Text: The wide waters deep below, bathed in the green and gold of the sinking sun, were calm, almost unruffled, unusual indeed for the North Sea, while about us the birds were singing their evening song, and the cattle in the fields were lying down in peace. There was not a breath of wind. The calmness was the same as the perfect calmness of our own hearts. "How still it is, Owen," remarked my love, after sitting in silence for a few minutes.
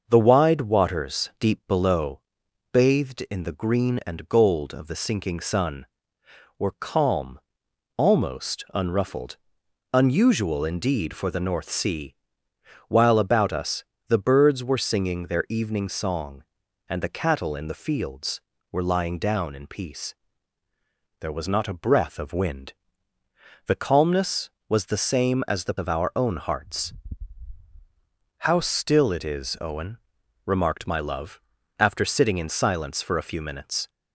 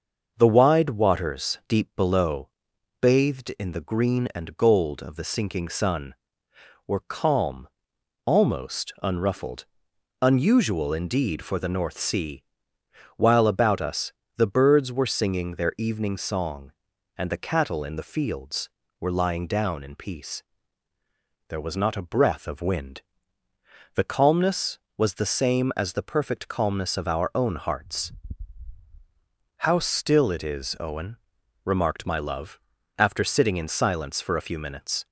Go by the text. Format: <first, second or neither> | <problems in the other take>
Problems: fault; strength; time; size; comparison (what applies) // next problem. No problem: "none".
second | starts louder than the rest; until 1.0 s; 6.5 dB; also in the second // pauses between "us" and "the"; slight; at 13.8 s; 0.24 s long; slight in the second // skips "perfect calmness"; at 25.7 s